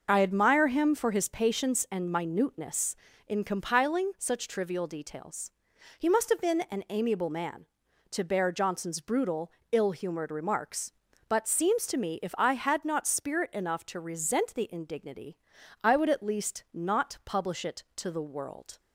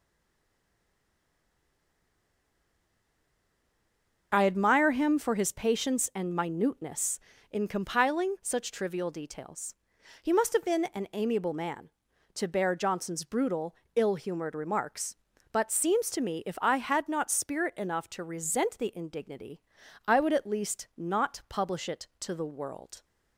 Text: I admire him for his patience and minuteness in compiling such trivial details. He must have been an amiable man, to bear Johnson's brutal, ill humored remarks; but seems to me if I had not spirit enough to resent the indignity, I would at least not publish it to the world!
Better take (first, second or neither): first